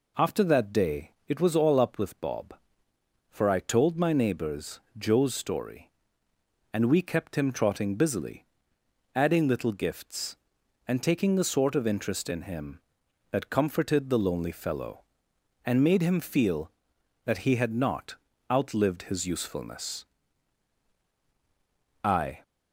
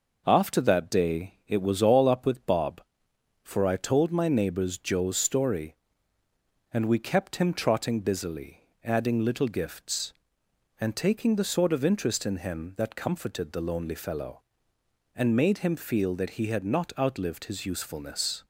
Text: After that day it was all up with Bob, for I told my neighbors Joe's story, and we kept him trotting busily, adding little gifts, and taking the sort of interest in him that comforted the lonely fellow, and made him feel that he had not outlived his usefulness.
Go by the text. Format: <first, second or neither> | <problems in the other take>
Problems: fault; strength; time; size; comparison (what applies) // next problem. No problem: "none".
second | pauses between "neighbors" and "Joe's"; slight; at 4.8 s; 0.18 s long // pauses between "not" and "outlived"; slight; at 18.1 s; 0.34 s long // goes on to say "I"; slight; from 22.0 s on; 0.38 s long